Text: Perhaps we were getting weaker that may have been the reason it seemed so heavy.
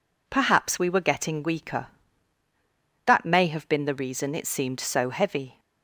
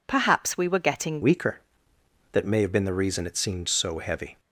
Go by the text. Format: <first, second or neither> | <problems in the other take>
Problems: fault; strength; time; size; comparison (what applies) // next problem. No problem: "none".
first | changes voice at "weaker"; from 1.2 s on; 3.1 s long